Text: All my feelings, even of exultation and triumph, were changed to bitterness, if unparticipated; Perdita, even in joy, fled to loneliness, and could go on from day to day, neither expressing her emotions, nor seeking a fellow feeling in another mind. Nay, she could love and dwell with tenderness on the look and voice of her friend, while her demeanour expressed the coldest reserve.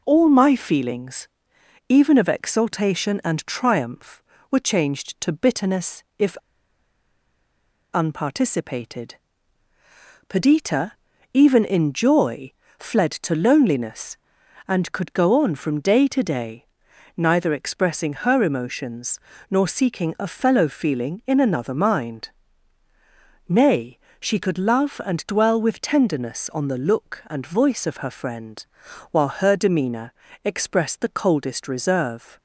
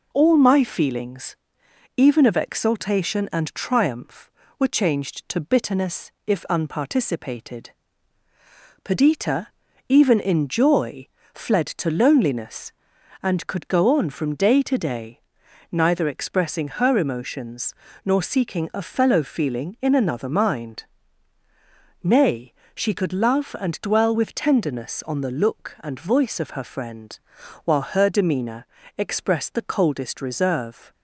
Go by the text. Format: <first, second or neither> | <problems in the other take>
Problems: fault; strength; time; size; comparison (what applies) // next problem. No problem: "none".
second | pauses between "if" and "unparticipated"; strong; at 6.3 s; 1.5 s long // pauses between "demeanour" and "expressed"; slight; at 30.1 s; 0.30 s long; slight in the second